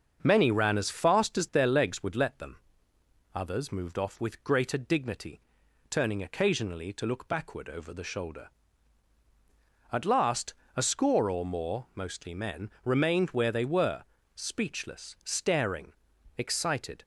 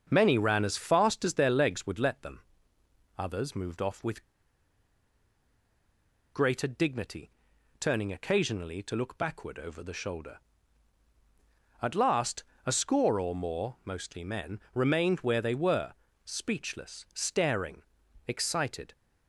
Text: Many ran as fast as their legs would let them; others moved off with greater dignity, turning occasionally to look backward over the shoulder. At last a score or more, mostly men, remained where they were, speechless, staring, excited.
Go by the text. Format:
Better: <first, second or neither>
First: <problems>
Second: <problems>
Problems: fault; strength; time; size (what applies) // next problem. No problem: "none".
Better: first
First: starts louder than the rest; until 1.2 s; 6.5 dB // pauses between "last" and "a"; slight; at 10.5 s; 0.20 s long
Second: starts louder than the rest; until 1.1 s; 6.5 dB // pauses between "with" and "greater"; strong; at 4.2 s; 2.0 s long // pauses between "last" and "a"; slight; at 12.4 s; 0.20 s long